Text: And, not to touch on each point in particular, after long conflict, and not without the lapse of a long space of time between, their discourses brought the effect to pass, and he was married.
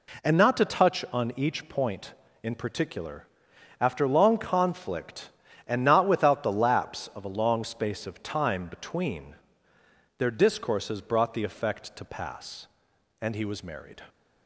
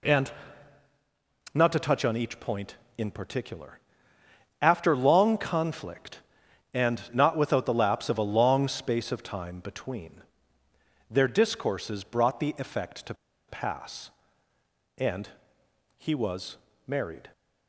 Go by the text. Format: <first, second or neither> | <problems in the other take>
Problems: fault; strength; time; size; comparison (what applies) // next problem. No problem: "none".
first | pauses between "to" and "pass"; slight; at 13.1 s; 0.34 s long // pauses between "and" and "he"; noticeable; at 15.2 s; 0.66 s long // pauses between "was" and "married"; slight; at 16.5 s; 0.28 s long